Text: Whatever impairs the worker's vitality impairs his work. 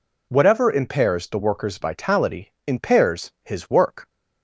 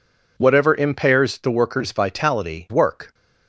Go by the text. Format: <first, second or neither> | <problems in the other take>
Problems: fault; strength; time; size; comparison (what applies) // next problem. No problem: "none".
first | skips "impairs his"; at 2.6 s